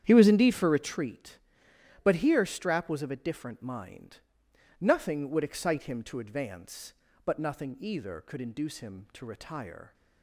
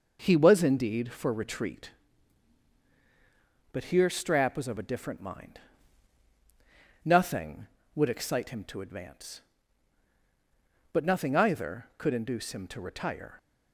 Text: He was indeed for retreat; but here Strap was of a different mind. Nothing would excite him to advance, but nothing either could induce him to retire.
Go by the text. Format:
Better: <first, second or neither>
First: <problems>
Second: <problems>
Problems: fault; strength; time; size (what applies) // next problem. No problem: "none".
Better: second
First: starts louder than the rest; strong; until 1.0 s; 9 dB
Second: none